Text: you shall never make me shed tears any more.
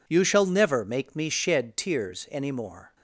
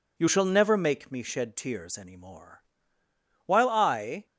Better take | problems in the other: first | goes on to say "While I"; noticeable; from 3.4 s on; 0.80 s long

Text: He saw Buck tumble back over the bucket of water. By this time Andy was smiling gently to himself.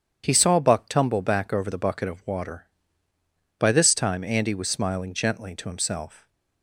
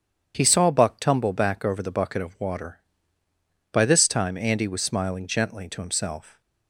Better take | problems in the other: neither | starts louder than the rest; strong; the same in both

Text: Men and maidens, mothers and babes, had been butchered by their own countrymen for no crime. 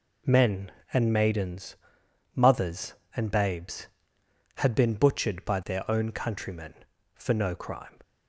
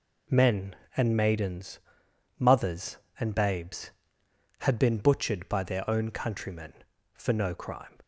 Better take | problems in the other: neither | none

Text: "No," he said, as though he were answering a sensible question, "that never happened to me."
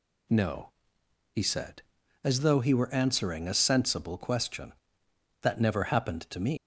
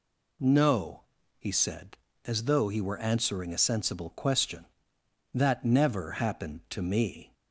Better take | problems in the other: second | leaves "me" unfinished; at 6.5 s; 145 ms

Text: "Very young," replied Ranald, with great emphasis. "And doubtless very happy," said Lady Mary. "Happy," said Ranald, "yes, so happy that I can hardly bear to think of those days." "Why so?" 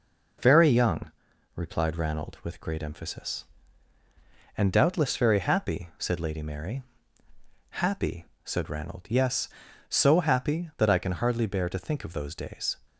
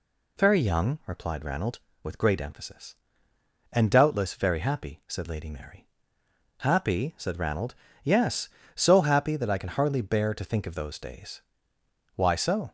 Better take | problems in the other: second | stops before "Why so"; at 12.8 s

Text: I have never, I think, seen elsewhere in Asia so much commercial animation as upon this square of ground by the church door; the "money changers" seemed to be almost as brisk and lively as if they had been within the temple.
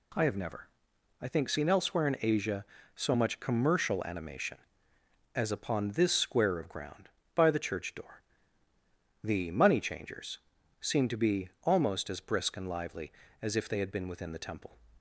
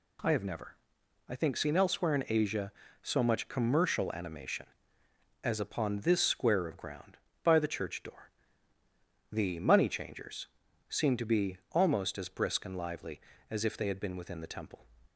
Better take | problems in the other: neither | pauses between "changers" and "seemed"; the same in both // pauses between "be" and "almost"; slight; the same in both

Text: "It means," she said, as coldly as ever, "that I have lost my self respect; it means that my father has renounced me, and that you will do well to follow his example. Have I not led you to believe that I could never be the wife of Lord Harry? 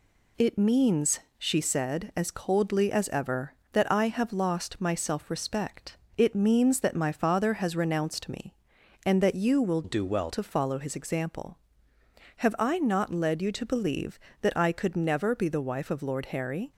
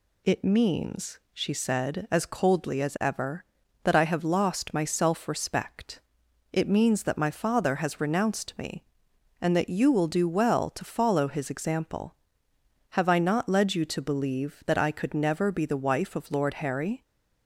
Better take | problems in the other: second | changes voice from "do" to "well"; from 9.8 to 10.2 s; 0.4 s long

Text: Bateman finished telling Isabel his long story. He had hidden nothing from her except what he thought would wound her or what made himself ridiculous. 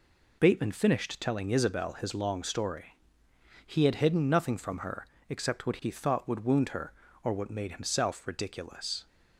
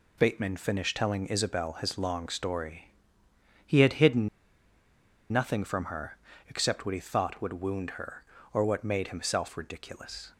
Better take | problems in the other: first | pauses between "hidden" and "nothing"; at 4.2 s; 1.0 s long // pauses between "her" and "except"; slight; at 6.1 s; 0.32 s long; slight in the first

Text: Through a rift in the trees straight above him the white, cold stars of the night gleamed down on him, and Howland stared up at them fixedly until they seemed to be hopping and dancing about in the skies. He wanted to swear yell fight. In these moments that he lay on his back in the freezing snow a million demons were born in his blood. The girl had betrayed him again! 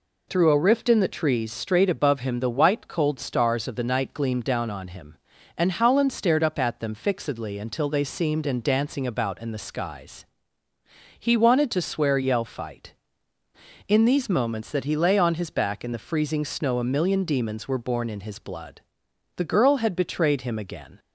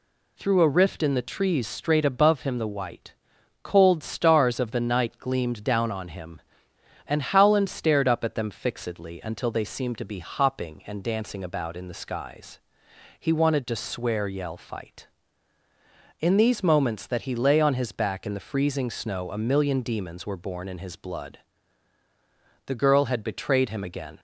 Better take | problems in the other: second | skips "to be hopping"; at 8.4 s

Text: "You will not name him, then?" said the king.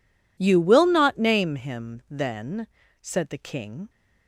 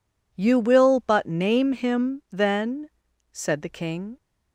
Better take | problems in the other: first | says "but" for "not"; at 1.0 s

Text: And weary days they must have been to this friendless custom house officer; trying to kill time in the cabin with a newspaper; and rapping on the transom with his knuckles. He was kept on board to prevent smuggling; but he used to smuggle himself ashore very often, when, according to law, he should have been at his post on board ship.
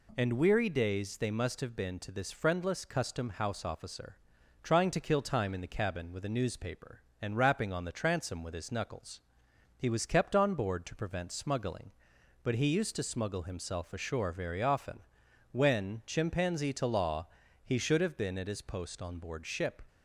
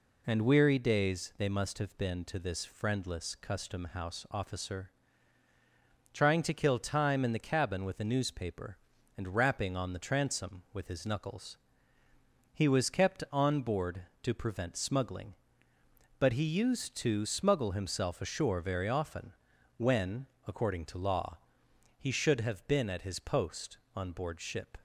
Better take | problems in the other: second | says "chimpanzee" for "according"; at 16.0 s

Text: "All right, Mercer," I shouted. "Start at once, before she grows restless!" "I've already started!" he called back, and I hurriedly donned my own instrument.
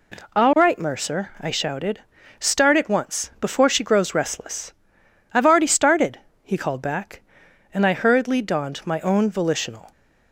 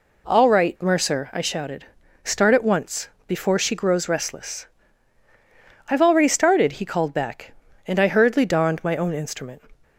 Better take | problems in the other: second | says "volitional" for "instrument"; at 9.2 s

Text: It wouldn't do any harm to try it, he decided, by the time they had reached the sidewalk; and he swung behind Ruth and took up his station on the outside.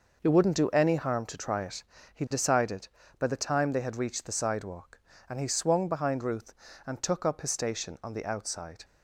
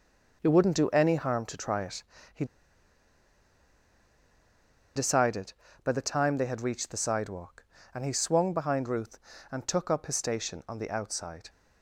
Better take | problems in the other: first | pauses between "he" and "decided"; strong; at 2.4 s; 2.5 s long

